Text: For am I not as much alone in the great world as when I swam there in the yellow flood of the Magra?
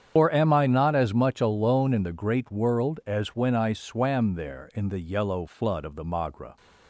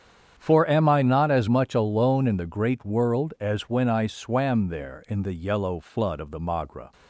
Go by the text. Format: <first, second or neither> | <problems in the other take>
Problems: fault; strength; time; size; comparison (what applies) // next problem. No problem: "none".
second | loses the start of "For"; at 0.1 s; 135 ms // starts louder than the rest; strong; until 1.1 s; 8.5 dB; strong in the second